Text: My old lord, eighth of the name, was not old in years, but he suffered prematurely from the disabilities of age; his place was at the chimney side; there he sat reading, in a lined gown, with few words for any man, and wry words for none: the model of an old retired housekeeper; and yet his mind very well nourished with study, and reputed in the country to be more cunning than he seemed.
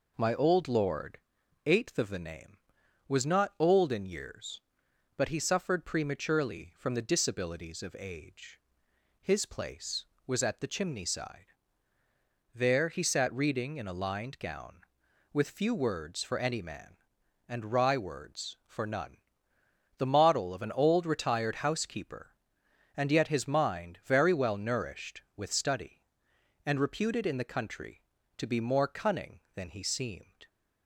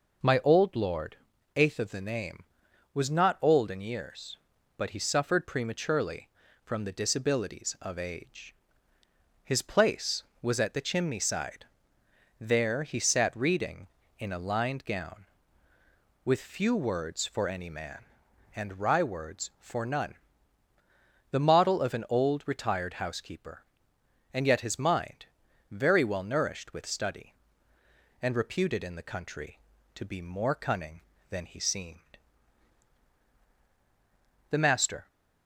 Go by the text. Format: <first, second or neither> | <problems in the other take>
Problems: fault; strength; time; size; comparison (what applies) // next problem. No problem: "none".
first | pauses between "mind" and "very"; noticeable; at 25.2 s; 0.46 s long // goes on to say "The Master"; from 34.5 s on; 0.56 s long